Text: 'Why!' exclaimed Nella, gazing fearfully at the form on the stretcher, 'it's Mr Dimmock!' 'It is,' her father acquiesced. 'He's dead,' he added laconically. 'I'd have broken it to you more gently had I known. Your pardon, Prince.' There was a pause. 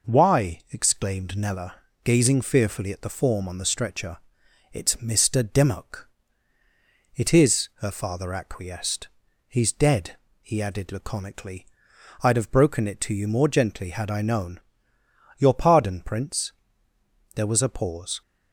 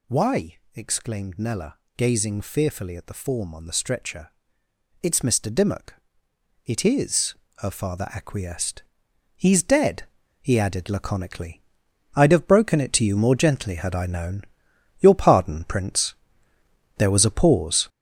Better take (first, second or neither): first